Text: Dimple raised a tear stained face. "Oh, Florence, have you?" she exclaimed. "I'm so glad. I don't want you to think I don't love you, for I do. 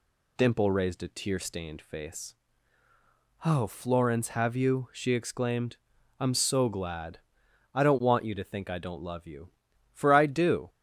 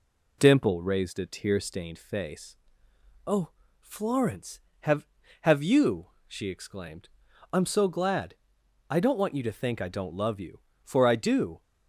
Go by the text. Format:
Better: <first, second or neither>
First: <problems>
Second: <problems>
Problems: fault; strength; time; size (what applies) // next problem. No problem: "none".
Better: first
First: none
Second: says "have" twice; at 5.4 s